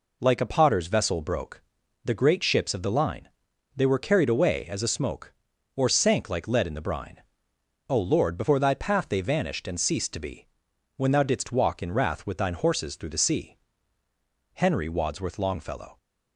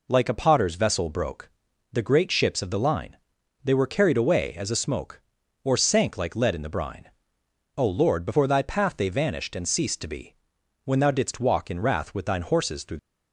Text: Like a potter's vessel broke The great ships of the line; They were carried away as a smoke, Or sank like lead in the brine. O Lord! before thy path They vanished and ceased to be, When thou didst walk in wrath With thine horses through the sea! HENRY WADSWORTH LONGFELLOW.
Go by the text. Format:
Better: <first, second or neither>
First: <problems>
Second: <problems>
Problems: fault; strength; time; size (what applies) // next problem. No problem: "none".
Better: first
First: pauses between "broke" and "The"; at 1.6 s; 0.44 s long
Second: pauses between "broke" and "The"; at 1.4 s; 0.44 s long // stops before "the sea HENRY WADSWORTH LONGFELLOW"; at 12.9 s